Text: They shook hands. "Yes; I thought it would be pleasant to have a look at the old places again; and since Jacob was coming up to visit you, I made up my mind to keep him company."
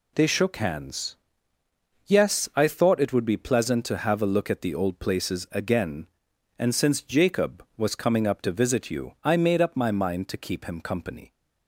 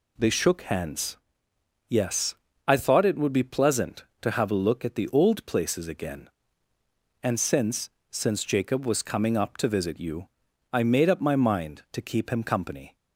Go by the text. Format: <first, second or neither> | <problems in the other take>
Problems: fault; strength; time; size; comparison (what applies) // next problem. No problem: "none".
first | says "since" twice; at 8.0 s